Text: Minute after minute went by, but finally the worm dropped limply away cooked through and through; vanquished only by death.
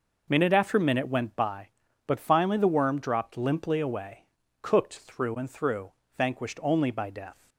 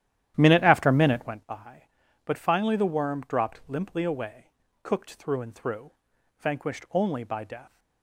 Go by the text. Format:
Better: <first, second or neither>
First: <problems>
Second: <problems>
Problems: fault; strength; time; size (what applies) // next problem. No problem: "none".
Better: first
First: pauses between "away" and "cooked"; slight; at 4.2 s; 0.34 s long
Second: starts louder than the rest; strong; until 1.4 s; 11.5 dB // pauses between "away" and "cooked"; at 4.4 s; 0.36 s long